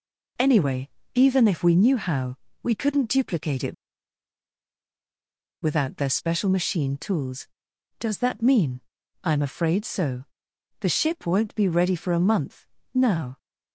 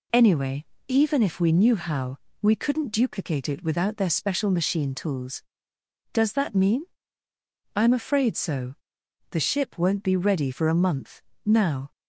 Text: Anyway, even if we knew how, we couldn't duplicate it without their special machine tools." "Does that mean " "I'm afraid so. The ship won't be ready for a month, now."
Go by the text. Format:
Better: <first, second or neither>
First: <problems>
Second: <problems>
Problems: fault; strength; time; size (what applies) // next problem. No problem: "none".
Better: second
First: pauses between "it" and "without"; strong; at 3.7 s; 1.8 s long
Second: none